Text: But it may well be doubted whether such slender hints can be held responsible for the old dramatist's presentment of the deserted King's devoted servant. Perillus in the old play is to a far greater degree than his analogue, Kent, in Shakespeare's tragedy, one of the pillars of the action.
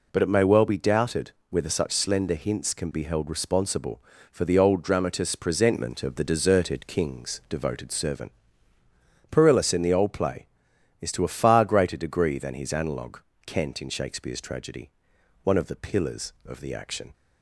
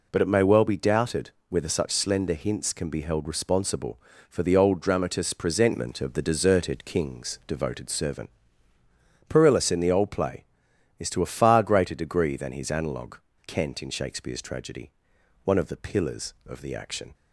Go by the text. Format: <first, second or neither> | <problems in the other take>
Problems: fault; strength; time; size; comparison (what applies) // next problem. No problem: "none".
neither | pauses between "doubted" and "whether"; slight; the same in both